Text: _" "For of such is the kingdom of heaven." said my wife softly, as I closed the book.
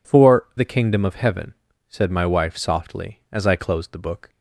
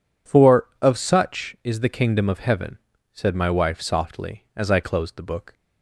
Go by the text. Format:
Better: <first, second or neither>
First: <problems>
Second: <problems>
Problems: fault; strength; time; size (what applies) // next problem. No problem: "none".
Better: second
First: skips "of such is"; at 0.5 s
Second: none